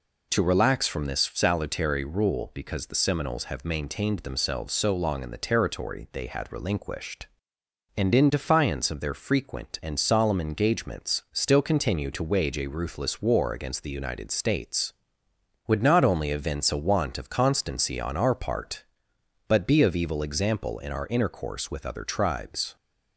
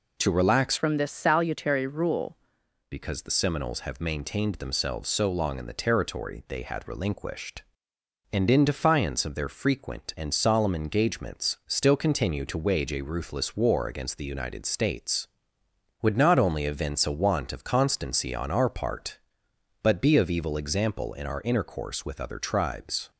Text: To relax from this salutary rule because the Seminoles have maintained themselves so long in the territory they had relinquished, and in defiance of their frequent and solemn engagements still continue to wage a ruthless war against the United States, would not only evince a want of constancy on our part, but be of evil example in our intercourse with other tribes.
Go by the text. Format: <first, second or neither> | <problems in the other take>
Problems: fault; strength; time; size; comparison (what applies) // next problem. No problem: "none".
first | changes voice from "from" to "rule"; from 0.7 to 2.3 s; 1.6 s long